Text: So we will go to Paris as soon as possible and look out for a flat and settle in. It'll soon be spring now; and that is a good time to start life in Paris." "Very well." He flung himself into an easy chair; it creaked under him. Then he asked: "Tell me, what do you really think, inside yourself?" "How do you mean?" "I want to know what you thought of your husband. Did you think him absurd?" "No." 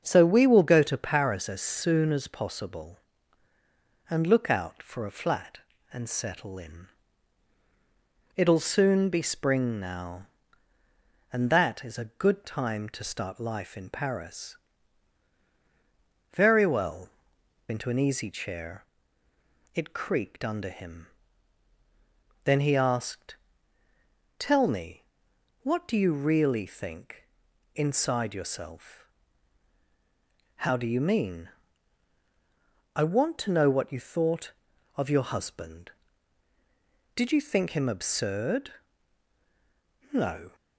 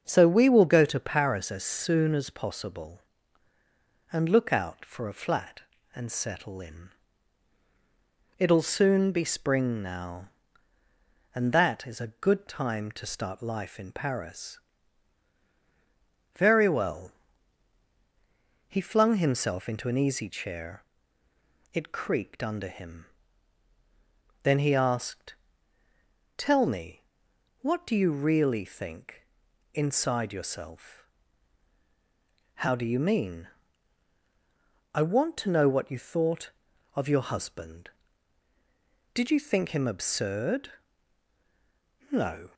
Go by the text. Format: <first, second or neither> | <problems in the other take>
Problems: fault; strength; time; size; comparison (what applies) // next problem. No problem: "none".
second | starts louder than the rest; until 1.0 s; 7 dB; also in the second // skips "He flung himself"; at 17.3 s